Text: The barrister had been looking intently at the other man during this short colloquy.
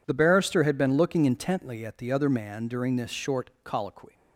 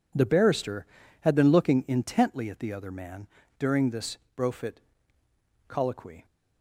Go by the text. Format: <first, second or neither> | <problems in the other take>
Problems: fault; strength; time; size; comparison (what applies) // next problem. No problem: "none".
first | pauses between "man" and "during"; slight; at 3.2 s; 0.32 s long // says "brofit" for "short"; at 4.3 s